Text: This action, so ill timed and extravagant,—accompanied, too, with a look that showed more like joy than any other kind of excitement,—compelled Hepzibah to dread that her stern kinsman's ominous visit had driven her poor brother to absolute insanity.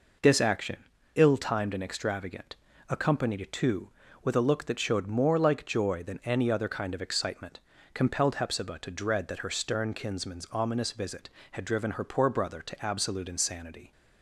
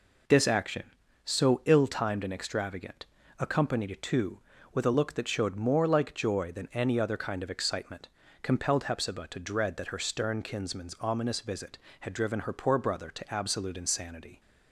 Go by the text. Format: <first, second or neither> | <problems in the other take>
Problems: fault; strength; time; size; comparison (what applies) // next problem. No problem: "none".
second | skips "so"; at 0.9 s